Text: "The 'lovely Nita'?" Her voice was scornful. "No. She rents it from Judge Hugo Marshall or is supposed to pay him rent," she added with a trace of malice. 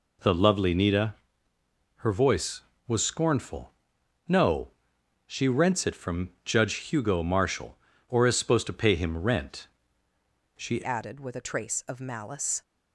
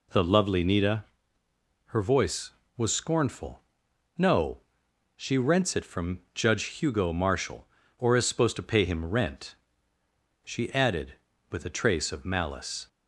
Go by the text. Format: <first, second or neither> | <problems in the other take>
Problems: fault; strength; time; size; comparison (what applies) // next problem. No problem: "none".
second | changes voice at "added"; from 10.8 s on; 1.8 s long